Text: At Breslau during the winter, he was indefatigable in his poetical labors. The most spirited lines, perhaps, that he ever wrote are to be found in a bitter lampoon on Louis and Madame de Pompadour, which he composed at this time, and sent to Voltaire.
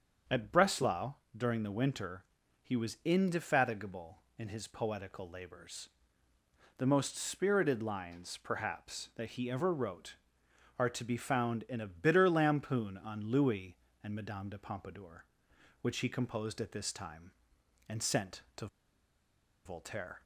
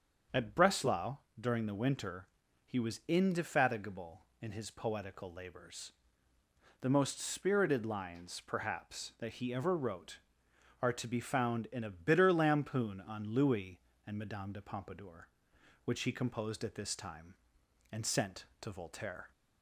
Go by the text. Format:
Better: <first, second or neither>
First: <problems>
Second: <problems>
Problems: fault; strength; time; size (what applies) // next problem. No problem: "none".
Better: second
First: starts louder than the rest; strong; until 1.5 s; 7 dB // pauses between "Breslau" and "during"; slight; at 1.1 s; 0.22 s long // pauses between "to" and "Voltaire"; at 18.6 s; 0.98 s long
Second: starts louder than the rest; strong; until 1.5 s; 7 dB // pauses between "Breslau" and "during"; slight; at 1.1 s; 0.22 s long